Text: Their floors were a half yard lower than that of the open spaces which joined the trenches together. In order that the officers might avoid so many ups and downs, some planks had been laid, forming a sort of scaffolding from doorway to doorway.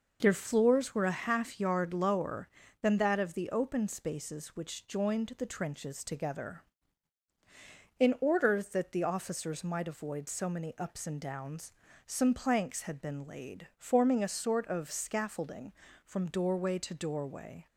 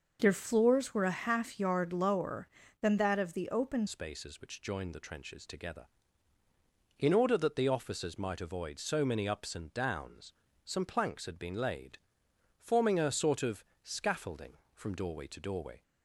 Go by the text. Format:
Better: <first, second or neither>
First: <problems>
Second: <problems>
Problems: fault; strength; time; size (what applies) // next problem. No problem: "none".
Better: first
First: none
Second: changes voice at "spaces"; from 3.8 s on; 12.0 s long // pauses between "of" and "scaffolding"; slight; at 13.6 s; 0.20 s long